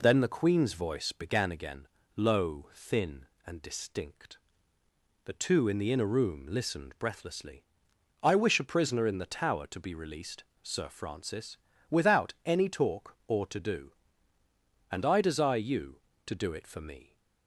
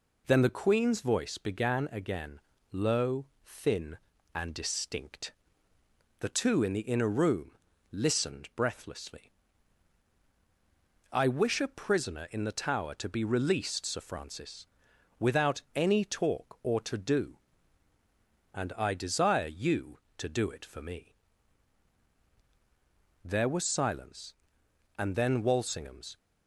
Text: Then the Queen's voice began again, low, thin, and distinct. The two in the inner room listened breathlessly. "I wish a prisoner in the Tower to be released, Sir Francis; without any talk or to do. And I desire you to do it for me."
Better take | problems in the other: first | pauses between "room" and "listened"; at 7.5 s; 0.40 s long // goes on to say "There was silence and then Walsingham's"; strong; from 23.2 s on; 2.9 s long

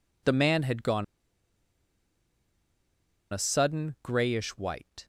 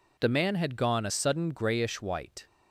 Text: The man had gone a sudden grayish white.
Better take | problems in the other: second | pauses between "gone" and "a"; strong; at 1.0 s; 2.2 s long

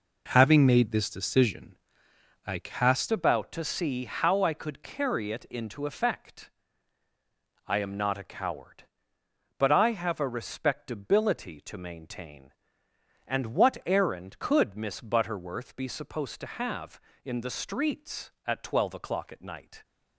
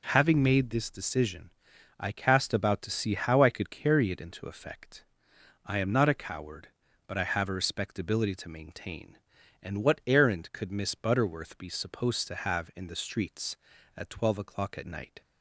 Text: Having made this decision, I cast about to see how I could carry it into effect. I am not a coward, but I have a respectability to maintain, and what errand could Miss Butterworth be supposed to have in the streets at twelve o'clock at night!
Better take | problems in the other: second | changes voice at "about"; from 3.1 s on; 16.7 s long

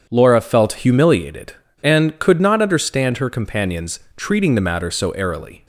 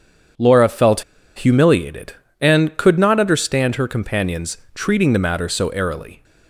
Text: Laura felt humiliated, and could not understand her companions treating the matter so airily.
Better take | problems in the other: first | starts louder than the rest; strong; until 1.7 s; 8 dB; strong in the first // pauses between "felt" and "humiliated"; slight; at 1.0 s; 0.34 s long // pauses between "companions" and "treating"; slight; at 4.5 s; 0.16 s long; slight in the first

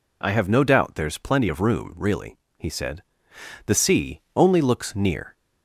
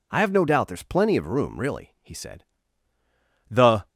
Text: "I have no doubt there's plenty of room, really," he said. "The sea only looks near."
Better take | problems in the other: first | stops before "sea only looks near"; at 3.8 s

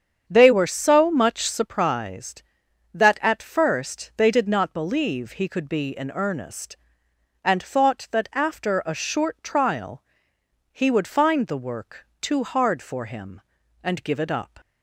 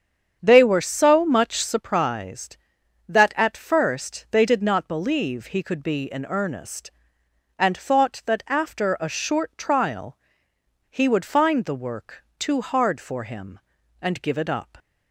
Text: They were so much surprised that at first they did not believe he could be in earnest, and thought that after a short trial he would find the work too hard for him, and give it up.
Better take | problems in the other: neither | starts louder than the rest; strong; the same in both // pauses between "trial" and "he"; noticeable; the same in both // pauses between "work" and "too"; slight; the same in both

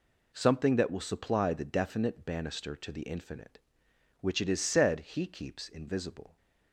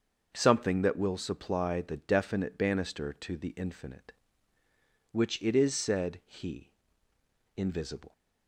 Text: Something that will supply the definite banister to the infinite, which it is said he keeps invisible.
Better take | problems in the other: first | starts louder than the rest; until 1.3 s; 6.5 dB // skips "keeps"; at 7.1 s

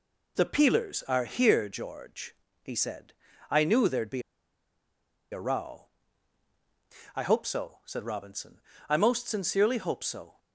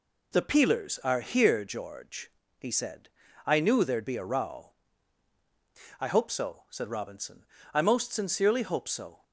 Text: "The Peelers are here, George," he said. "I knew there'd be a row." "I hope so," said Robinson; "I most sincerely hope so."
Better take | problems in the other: second | pauses between "be" and "a"; at 4.2 s; 1.1 s long

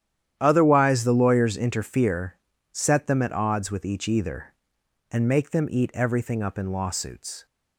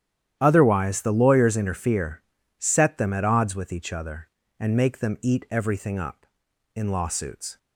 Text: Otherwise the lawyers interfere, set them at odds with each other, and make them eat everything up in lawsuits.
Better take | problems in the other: second | starts louder than the rest; strong; until 1.4 s; 10.5 dB; strong in the second // says "either" for "other"; at 4.0 s

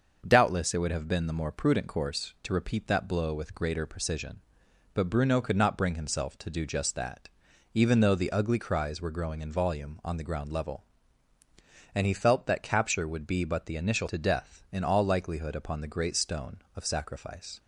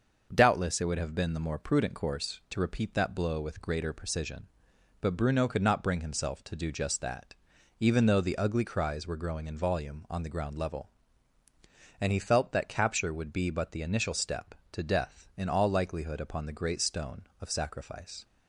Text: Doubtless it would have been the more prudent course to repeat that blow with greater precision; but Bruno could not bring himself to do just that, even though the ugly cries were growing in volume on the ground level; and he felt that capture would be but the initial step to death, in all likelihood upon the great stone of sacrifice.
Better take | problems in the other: second | starts louder than the rest; until 1.2 s; 6.5 dB; also in the second // skips "step"; at 14.0 s

